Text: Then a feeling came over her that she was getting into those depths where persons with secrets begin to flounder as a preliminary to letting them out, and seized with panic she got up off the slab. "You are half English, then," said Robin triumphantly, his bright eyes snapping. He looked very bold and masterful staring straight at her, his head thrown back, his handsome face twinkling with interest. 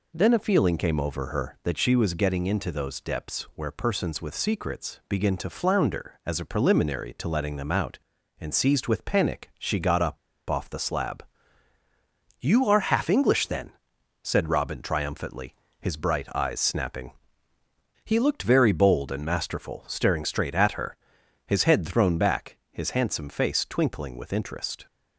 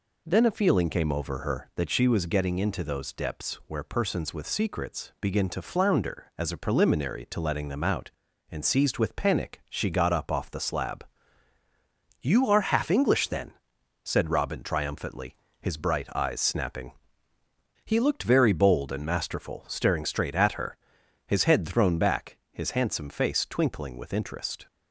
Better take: second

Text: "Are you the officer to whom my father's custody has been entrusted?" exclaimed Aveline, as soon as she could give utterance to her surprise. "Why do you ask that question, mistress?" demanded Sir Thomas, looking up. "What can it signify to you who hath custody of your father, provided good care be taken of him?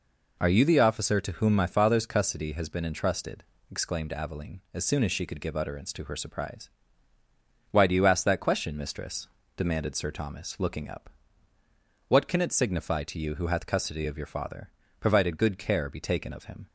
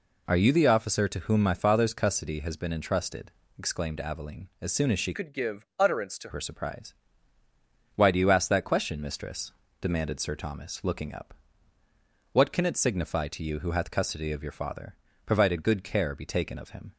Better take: first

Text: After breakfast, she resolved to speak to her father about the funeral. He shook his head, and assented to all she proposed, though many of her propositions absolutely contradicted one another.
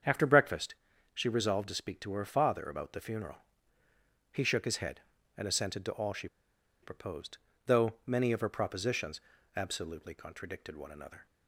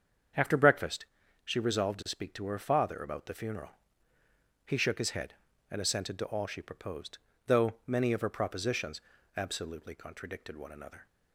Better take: second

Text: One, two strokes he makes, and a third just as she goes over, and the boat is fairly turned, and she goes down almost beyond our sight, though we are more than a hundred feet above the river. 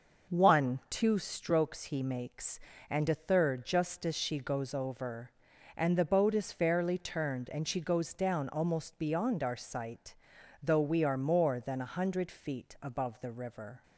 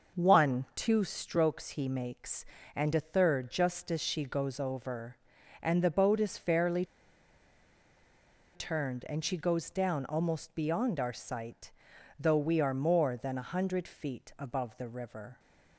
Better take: first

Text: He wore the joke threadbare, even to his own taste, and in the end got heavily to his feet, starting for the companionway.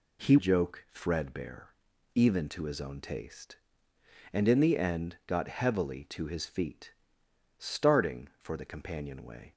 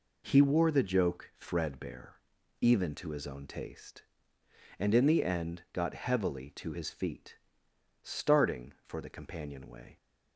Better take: second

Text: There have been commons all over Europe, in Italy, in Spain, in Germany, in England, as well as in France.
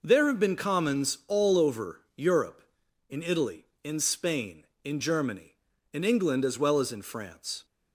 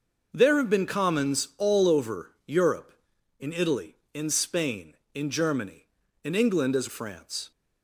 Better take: first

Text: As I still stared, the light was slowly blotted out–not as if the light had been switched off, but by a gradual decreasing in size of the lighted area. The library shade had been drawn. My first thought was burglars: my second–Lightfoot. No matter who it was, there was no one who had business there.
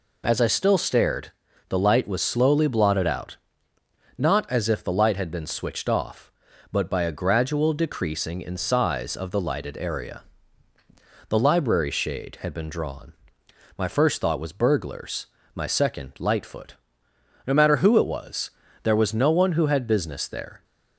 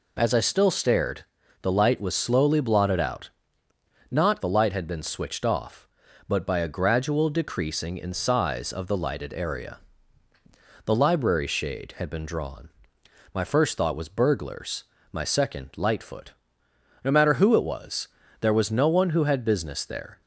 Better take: first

